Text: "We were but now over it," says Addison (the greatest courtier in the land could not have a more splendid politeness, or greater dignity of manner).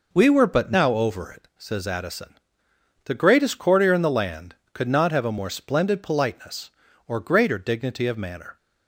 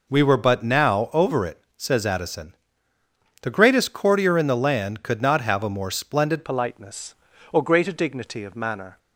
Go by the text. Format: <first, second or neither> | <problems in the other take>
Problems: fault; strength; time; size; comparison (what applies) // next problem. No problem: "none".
first | changes voice at "politeness"; from 6.4 s on; 2.5 s long